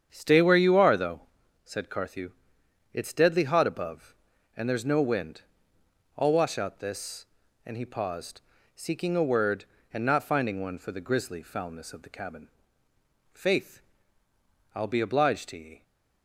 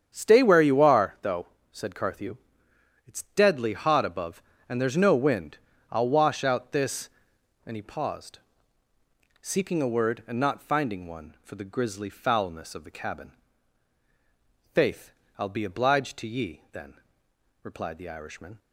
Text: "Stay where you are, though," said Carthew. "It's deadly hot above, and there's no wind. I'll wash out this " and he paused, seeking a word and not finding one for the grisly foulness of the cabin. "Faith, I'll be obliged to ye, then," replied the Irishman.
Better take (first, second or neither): second